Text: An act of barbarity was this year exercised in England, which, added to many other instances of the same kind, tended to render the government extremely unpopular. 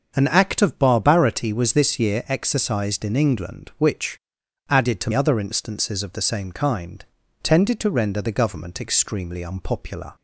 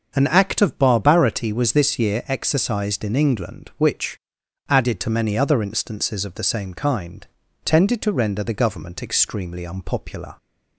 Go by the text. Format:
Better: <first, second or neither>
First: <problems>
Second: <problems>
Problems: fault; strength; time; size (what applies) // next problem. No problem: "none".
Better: second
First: starts louder than the rest; until 1.1 s; 6.5 dB // skips "many"; at 5.1 s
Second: starts louder than the rest; until 1.1 s; 6.5 dB